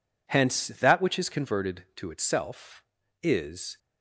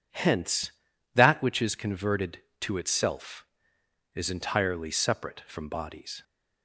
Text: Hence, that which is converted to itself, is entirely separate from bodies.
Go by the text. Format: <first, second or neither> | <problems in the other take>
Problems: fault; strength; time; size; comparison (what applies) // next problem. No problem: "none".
second | stops before "entirely separate from bodies"; at 3.7 s